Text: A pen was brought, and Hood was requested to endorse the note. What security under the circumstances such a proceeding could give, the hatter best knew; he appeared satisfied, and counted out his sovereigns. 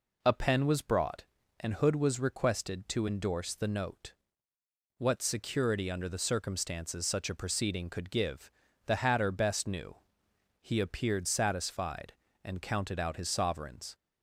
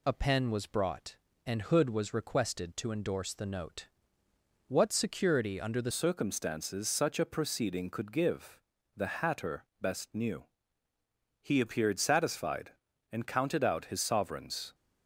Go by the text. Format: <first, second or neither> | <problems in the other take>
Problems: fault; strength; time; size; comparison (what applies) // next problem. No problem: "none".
first | changes voice at "circumstances"; from 5.9 s on; 8.8 s long // pauses between "hatter" and "best"; slight; at 9.6 s; 0.16 s long